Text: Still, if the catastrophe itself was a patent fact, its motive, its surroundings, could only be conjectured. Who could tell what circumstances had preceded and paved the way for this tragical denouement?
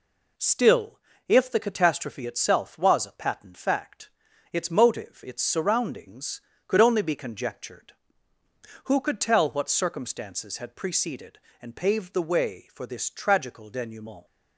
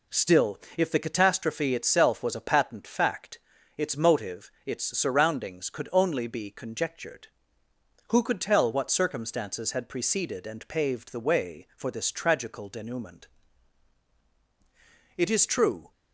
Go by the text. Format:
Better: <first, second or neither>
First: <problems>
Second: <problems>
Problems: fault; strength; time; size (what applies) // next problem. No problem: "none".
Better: first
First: none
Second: goes on to say "It is true"; noticeable; from 15.1 s on; 0.74 s long